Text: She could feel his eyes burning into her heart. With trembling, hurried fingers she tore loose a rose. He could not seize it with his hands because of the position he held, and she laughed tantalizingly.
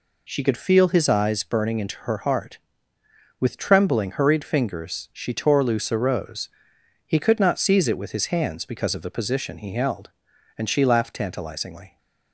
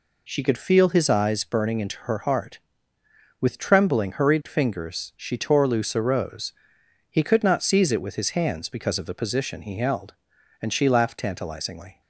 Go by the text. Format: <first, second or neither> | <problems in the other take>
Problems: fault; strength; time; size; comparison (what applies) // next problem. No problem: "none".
neither | none